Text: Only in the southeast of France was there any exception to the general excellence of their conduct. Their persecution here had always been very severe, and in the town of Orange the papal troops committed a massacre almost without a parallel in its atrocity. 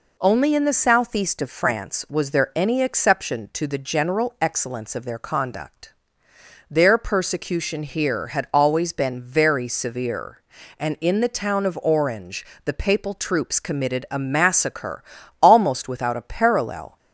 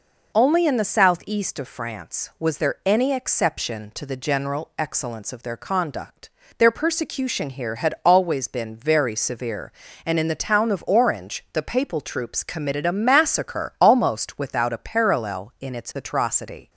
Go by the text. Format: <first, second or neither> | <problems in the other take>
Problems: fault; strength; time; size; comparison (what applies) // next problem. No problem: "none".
second | pauses between "Orange" and "the"; slight; at 12.4 s; 0.18 s long // pauses between "massacre" and "almost"; at 15.0 s; 0.38 s long // stops before "in its atrocity"; at 16.9 s